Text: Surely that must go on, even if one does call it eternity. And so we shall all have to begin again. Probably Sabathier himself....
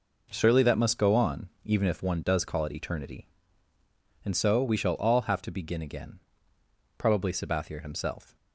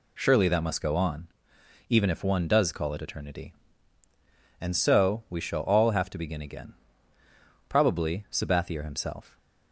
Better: neither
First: none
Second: none

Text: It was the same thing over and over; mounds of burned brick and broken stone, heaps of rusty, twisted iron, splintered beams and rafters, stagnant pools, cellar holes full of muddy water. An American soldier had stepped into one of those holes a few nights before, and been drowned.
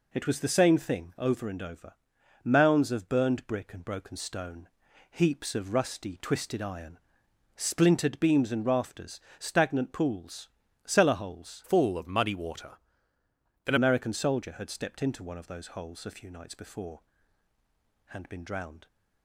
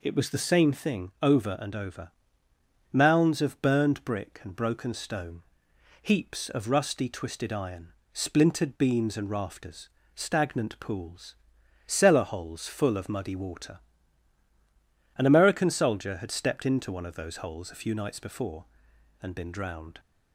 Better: second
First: changes voice from "full" to "An"; from 11.6 to 13.7 s; 2.1 s long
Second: none

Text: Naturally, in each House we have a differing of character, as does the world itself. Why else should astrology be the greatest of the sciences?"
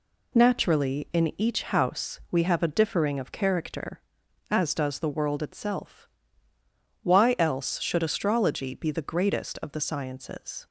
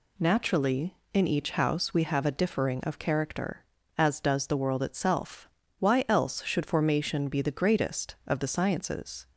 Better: first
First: none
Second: says "formation" for "astrology"; at 6.6 s

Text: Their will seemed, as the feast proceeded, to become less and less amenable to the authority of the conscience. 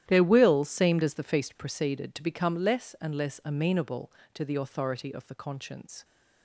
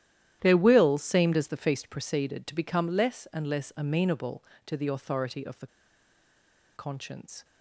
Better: first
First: starts louder than the rest; strong; until 1.0 s; 11.5 dB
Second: starts louder than the rest; strong; until 1.4 s; 11.5 dB // pauses between "the" and "conscience"; at 5.6 s; 1.0 s long

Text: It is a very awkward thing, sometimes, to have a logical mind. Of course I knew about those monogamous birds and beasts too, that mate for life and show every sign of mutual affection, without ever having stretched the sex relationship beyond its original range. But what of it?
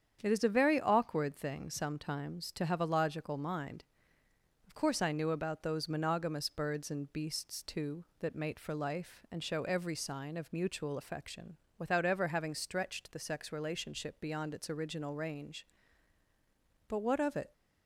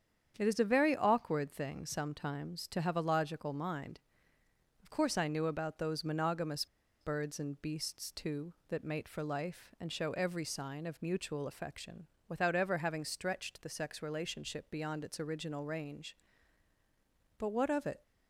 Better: first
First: starts louder than the rest; strong; until 1.2 s; 8 dB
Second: starts louder than the rest; strong; until 1.3 s; 8 dB // pauses between "monogamous" and "birds"; slight; at 6.6 s; 0.35 s long

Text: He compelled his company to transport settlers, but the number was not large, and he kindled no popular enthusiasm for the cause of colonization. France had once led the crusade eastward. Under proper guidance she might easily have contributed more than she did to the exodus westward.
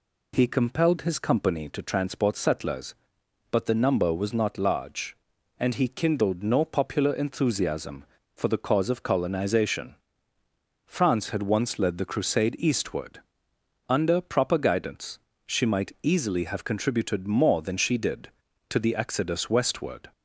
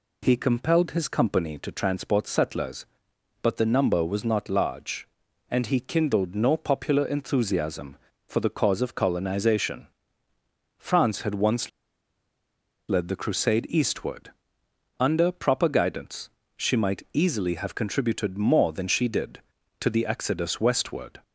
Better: first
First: pauses between "guidance" and "she"; slight; at 15.1 s; 0.28 s long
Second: pauses between "once" and "led"; at 11.6 s; 1.1 s long // pauses between "guidance" and "she"; slight; at 16.2 s; 0.28 s long

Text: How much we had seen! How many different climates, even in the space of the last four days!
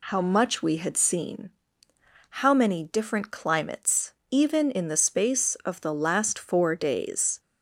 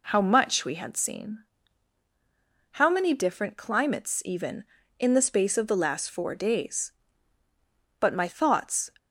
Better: first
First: none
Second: goes on to say "But my thoughts"; noticeable; from 8.0 s on; 0.90 s long

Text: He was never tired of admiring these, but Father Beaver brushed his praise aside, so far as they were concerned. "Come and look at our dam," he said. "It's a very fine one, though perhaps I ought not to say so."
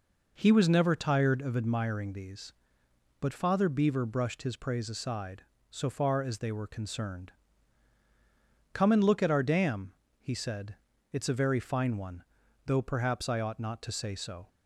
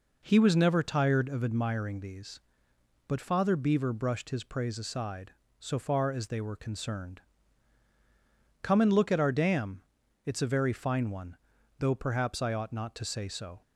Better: first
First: none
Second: skips "he said"; at 10.0 s

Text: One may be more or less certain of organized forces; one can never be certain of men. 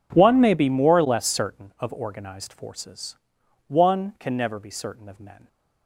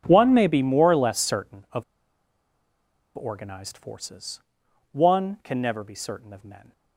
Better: first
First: none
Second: pauses between "of" and "organized"; strong; at 1.8 s; 1.3 s long

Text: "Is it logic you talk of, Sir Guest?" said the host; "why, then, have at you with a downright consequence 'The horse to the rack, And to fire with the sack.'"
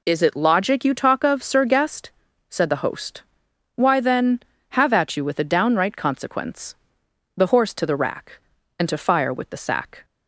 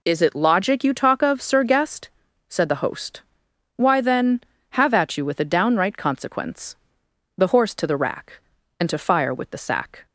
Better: neither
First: pauses between "consequence" and "The"; noticeable; at 6.7 s; 0.62 s long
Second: pauses between "consequence" and "The"; noticeable; at 6.7 s; 0.62 s long

